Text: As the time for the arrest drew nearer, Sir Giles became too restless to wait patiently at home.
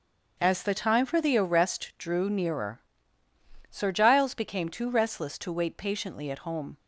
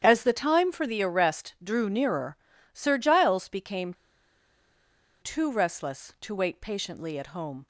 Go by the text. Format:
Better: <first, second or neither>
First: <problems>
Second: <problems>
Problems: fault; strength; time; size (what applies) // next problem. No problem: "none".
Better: first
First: starts louder than the rest; until 1.4 s; 6.5 dB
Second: starts louder than the rest; strong; until 1.0 s; 9.5 dB // pauses between "became" and "too"; strong; at 3.9 s; 1.2 s long